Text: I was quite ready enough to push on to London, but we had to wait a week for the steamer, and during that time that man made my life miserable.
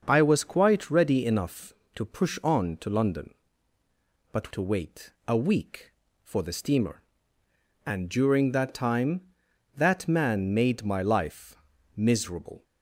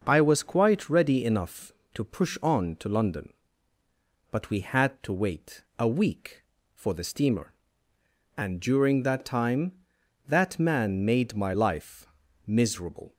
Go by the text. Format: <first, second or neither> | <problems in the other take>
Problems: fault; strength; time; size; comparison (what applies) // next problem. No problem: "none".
second | starts louder than the rest; until 1.0 s; 6.5 dB; noticeable in the second // skips "we had"; at 4.5 s // pauses between "wait" and "a"; slight; at 5.1 s; 0.16 s long; slight in the second // pauses between "life" and "miserable"; at 11.5 s; 0.40 s long; also in the second